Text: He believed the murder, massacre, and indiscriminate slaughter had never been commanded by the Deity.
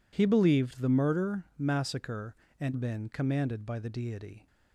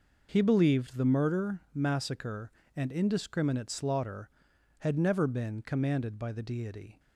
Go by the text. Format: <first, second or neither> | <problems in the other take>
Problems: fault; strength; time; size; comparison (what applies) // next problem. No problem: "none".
second | skips "indiscriminate slaughter had never"; at 2.7 s